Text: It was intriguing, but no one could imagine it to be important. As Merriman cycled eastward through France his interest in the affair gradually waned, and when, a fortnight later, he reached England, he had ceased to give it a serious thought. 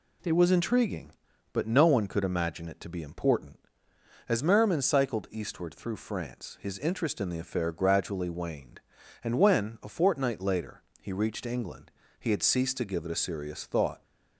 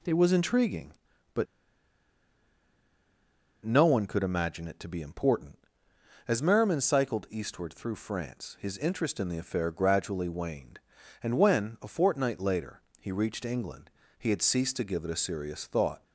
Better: first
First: none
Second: pauses between "but" and "no"; strong; at 1.4 s; 2.1 s long

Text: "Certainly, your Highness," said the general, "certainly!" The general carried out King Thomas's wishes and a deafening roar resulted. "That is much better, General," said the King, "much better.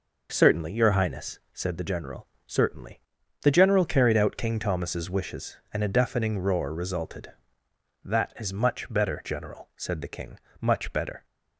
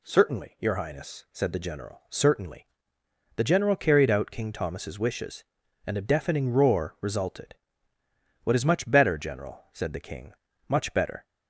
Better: first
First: none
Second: says "What" for "That"; at 8.4 s

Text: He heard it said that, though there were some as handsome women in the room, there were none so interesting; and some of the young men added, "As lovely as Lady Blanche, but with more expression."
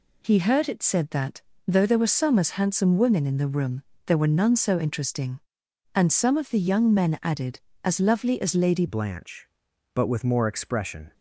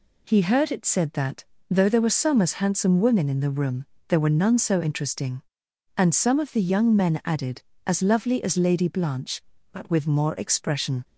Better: second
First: changes voice at "Blanche"; from 8.8 s on; 2.3 s long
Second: none

